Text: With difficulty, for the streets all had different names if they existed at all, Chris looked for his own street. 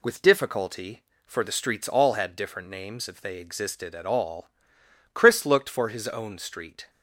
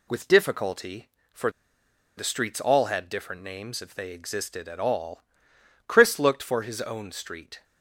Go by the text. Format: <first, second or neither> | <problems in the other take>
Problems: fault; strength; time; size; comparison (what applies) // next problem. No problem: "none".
first | pauses between "for" and "the"; noticeable; at 1.4 s; 0.67 s long